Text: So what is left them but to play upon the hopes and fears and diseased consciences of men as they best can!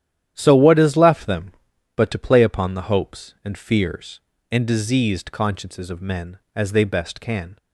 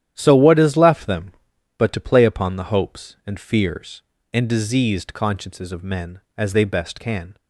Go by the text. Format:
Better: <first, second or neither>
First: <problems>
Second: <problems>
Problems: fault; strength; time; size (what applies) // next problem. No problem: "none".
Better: neither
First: starts louder than the rest; strong; until 1.3 s; 11 dB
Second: starts louder than the rest; strong; until 1.1 s; 11 dB